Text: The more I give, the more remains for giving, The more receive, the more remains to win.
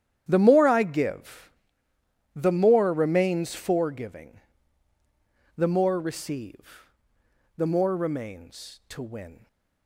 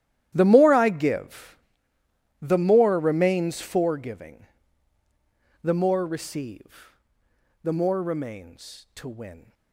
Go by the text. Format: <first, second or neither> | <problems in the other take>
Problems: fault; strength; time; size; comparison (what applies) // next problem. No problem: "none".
first | gets quieter; strong; throughout; 18 dB // starts louder than the rest; strong; until 1.3 s; 12 dB; strong in the first